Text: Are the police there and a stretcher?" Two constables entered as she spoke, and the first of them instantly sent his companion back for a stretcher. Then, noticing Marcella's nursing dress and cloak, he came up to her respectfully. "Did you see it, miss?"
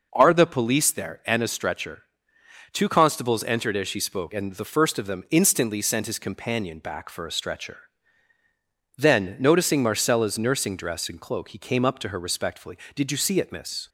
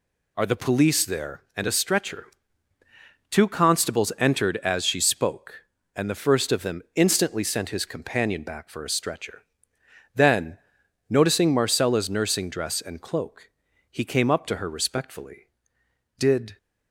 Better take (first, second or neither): first